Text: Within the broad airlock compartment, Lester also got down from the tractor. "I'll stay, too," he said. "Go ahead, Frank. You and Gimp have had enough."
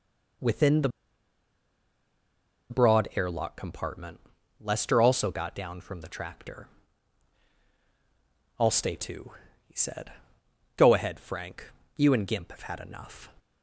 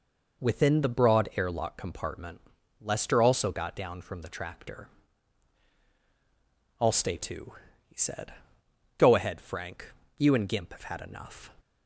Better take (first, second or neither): second